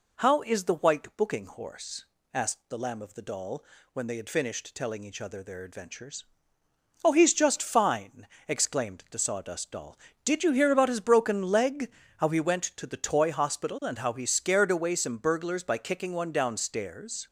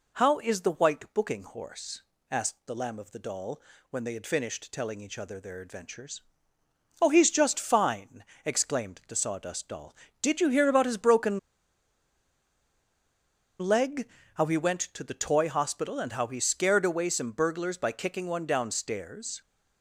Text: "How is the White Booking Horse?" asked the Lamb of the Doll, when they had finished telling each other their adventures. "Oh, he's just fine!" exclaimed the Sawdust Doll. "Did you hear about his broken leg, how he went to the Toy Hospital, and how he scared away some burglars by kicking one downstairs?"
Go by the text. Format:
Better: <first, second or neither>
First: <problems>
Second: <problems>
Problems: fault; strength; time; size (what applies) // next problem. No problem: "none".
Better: first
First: none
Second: pauses between "broken" and "leg"; strong; at 11.3 s; 2.2 s long